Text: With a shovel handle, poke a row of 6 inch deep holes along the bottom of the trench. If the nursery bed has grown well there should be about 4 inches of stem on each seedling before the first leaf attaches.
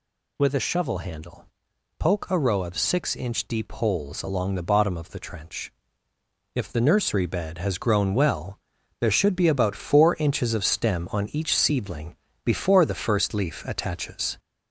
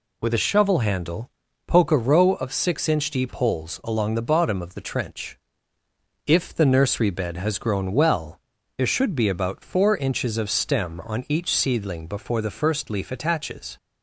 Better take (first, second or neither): second